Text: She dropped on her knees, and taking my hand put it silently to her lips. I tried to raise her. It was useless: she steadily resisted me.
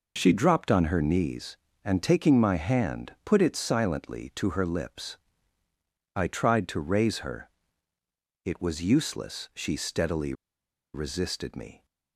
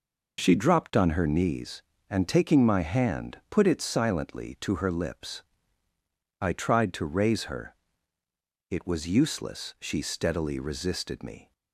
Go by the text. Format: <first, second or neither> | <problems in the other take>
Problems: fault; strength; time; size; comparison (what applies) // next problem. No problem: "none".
second | pauses between "steadily" and "resisted"; noticeable; at 10.3 s; 0.61 s long